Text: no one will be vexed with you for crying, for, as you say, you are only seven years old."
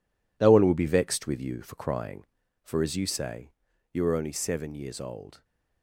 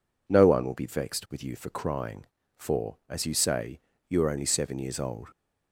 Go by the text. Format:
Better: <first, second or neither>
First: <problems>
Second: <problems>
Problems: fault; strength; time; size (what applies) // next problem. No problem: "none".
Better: second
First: gets quieter; strong; throughout; 10 dB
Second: none